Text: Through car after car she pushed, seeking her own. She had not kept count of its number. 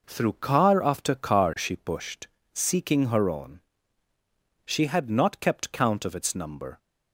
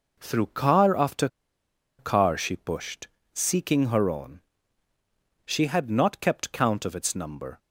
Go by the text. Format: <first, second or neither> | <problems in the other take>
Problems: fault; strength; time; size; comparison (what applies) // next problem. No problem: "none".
first | pauses between "after" and "car"; noticeable; at 1.2 s; 0.71 s long